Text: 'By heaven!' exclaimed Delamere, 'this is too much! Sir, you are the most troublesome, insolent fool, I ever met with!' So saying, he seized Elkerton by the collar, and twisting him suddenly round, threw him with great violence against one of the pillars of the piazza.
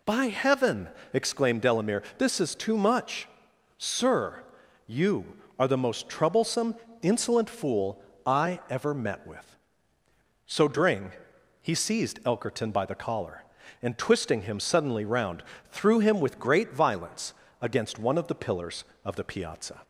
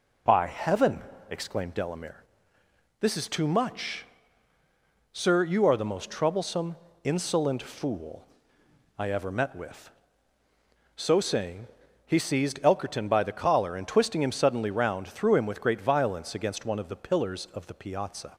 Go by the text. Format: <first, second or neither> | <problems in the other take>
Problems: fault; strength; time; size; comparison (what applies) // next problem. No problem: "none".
second | says "dring" for "saying"; at 10.6 s // pauses between "violence" and "against"; slight; at 17.3 s; 0.28 s long